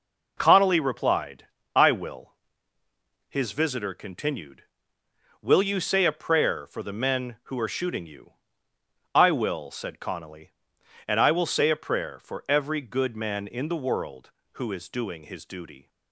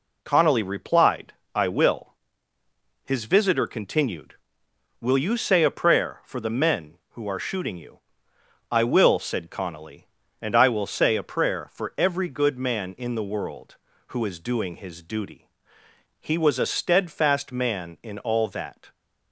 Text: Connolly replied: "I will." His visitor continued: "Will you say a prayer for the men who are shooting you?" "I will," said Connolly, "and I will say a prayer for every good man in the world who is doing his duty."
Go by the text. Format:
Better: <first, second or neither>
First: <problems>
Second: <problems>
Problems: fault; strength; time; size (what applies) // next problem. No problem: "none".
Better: first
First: none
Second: goes on to say "He was a steadfast man in all that"; strong; from 16.1 s on; 2.7 s long